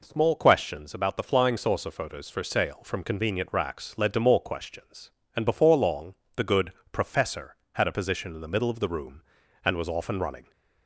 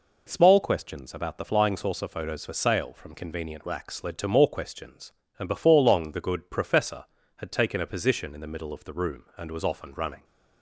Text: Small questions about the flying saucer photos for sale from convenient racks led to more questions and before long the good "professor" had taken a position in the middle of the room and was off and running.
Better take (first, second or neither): second